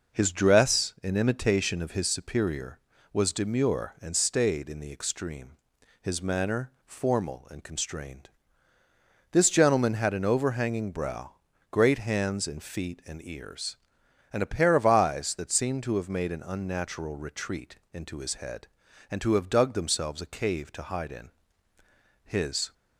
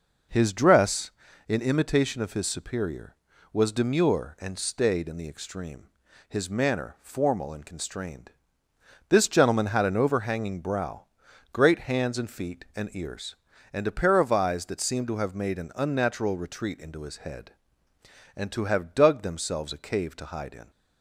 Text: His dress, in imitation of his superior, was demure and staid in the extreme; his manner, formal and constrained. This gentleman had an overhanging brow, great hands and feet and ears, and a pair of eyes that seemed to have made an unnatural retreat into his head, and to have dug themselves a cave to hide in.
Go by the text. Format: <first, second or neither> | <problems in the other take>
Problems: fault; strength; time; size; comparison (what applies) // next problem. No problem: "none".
second | goes on to say "His"; from 22.2 s on; 0.50 s long